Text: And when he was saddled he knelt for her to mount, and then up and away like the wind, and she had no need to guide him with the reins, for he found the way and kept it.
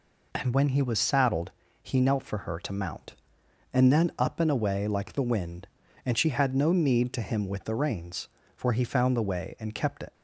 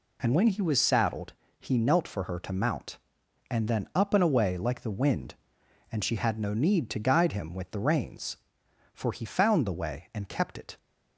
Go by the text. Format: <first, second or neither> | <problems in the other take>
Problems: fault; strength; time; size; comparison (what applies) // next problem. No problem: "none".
second | pauses between "saddled" and "he"; slight; at 1.5 s; 0.32 s long; slight in the second // skips "guide"; at 7.2 s